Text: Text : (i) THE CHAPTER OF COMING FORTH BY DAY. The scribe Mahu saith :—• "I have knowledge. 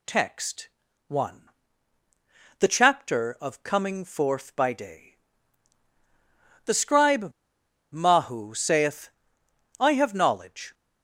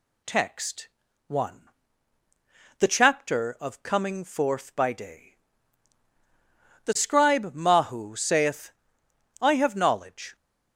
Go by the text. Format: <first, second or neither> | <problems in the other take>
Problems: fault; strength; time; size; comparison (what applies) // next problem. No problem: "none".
second | pauses between "scribe" and "Mahu"; noticeable; at 7.3 s; 0.60 s long